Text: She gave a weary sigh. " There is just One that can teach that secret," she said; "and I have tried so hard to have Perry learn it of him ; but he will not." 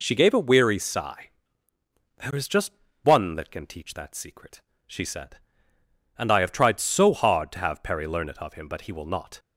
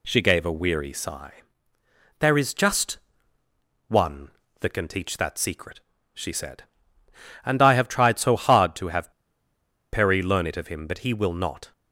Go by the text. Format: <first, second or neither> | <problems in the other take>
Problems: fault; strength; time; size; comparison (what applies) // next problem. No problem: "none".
first | pauses between "just" and "One"; noticeable; at 2.9 s; 0.90 s long; slight in the first // pauses between "have" and "Perry"; noticeable; at 9.0 s; 0.82 s long